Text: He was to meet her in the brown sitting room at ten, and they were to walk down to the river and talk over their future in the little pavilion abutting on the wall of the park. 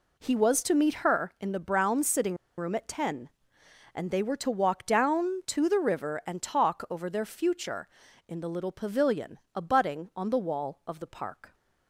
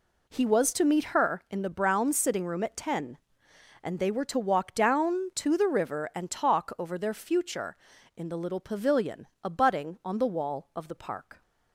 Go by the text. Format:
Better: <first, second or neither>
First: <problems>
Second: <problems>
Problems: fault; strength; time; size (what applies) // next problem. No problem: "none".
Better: second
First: pauses between "sitting" and "room"; slight; at 2.3 s; 0.21 s long // pauses between "pavilion" and "abutting"; slight; at 9.3 s; 0.16 s long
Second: pauses between "pavilion" and "abutting"; slight; at 9.2 s; 0.16 s long